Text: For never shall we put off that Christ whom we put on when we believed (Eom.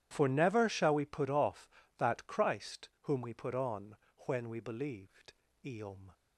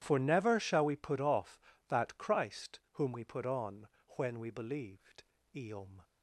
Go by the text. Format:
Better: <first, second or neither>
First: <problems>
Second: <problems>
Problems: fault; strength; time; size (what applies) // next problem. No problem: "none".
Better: neither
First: pauses between "on" and "when"; slight; at 3.9 s; 0.30 s long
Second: pauses between "on" and "when"; slight; at 3.8 s; 0.28 s long